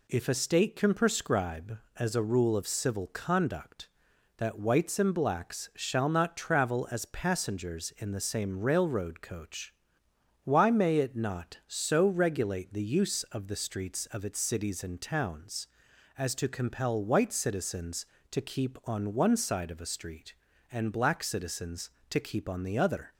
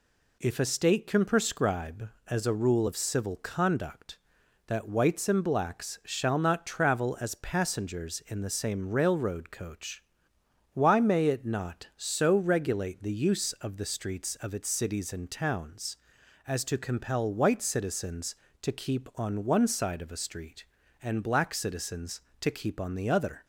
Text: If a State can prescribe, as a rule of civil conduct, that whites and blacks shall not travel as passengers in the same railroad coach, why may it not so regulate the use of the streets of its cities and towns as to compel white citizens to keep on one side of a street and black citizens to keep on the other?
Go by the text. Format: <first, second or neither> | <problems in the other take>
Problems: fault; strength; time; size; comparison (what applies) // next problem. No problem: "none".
neither | none